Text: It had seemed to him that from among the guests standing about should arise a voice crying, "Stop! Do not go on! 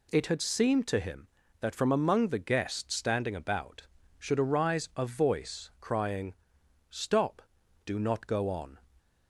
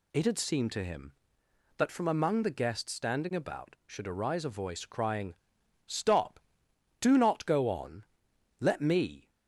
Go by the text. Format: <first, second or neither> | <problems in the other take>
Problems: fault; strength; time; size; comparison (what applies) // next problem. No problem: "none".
first | goes on to say "Let me"; noticeable; from 8.5 s on; 0.70 s long